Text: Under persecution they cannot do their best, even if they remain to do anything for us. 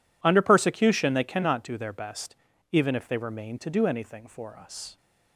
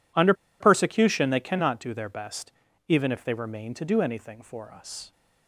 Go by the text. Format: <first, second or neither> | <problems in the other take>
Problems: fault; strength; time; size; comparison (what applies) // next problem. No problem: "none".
first | pauses between "Under" and "persecution"; slight; at 0.3 s; 0.27 s long